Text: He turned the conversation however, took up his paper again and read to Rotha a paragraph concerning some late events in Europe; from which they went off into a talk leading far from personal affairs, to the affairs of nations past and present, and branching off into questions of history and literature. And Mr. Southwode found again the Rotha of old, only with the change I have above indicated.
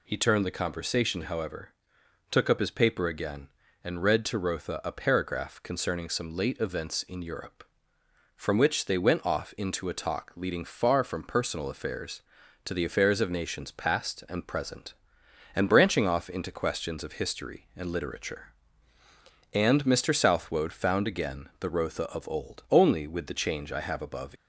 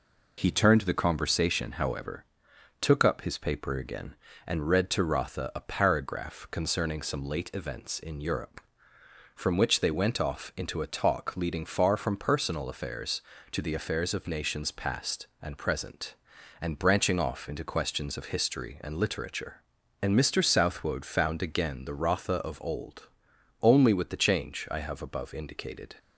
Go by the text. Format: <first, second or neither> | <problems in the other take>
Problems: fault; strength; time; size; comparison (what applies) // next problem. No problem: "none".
second | stops before "indicated"; at 24.3 s